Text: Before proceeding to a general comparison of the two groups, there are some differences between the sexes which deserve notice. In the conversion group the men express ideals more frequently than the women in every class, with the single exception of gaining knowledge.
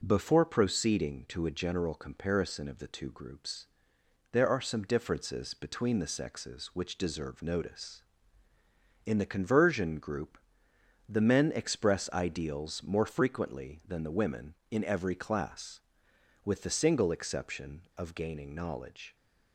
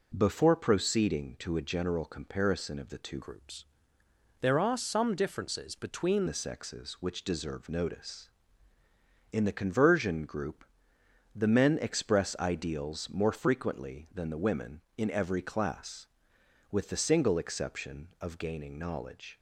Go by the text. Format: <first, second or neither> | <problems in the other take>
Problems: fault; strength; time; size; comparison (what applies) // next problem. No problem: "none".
first | changes voice from "groups" to "between"; from 3.2 to 6.2 s; 3.0 s long // pauses between "group" and "the"; noticeable; at 10.6 s; 0.70 s long; noticeable in the first